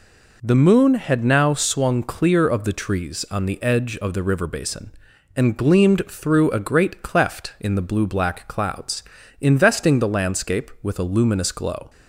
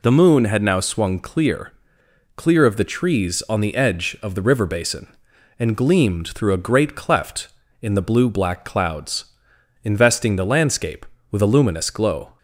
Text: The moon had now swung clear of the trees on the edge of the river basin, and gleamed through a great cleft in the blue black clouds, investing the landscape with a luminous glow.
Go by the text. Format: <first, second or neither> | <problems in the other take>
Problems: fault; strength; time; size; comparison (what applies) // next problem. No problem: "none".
first | says "clear" twice; at 2.3 s